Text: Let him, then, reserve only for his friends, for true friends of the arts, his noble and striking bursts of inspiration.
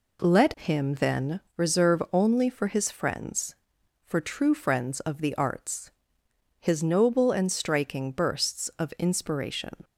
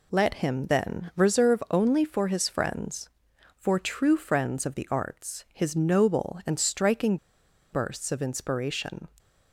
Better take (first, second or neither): first